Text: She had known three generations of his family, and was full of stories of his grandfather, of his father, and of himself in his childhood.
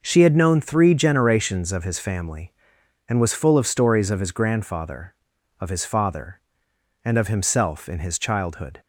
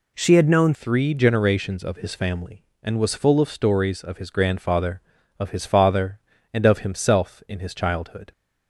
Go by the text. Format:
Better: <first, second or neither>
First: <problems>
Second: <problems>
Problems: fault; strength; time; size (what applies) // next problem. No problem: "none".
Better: first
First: none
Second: changes voice at "three"; from 0.7 s on; 7.6 s long